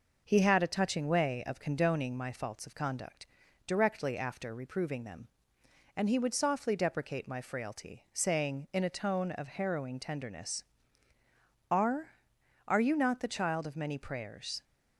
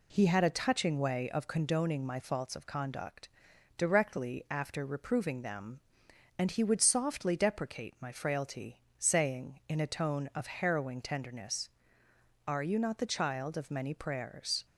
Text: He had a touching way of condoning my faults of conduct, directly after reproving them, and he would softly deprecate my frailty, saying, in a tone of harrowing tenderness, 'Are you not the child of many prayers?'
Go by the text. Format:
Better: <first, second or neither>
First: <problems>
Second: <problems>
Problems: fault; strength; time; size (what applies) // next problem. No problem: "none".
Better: second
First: says "Are" twice; at 12.6 s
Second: none